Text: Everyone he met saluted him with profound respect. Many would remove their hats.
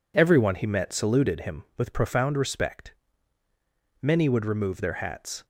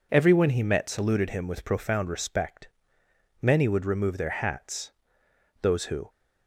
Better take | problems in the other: first | goes on to say "Those who"; slight; from 5.6 s on; 0.48 s long

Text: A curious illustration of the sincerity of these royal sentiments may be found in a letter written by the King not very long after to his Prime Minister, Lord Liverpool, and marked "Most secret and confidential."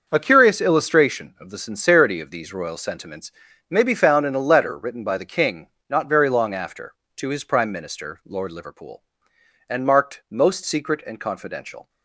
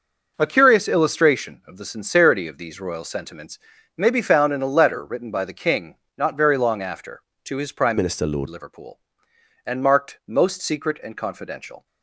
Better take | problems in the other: first | starts louder than the rest; noticeable; until 1.3 s; 6 dB; also in the first // pauses between "sentiments" and "may"; slight; at 3.6 s; 0.36 s long; slight in the first // pauses between "King" and "not"; slight; at 5.9 s; 0.24 s long; slight in the first // changes voice from "Minister" to "Lord"; from 7.9 to 8.4 s; 0.5 s long

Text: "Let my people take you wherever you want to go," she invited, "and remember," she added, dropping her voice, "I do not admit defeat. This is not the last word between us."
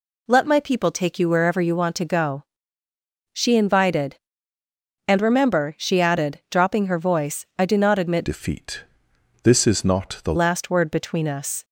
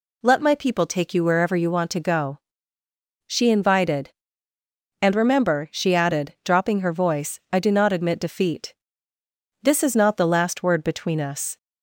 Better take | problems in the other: second | changes voice from "defeat" to "the"; from 8.2 to 10.3 s; 2.1 s long

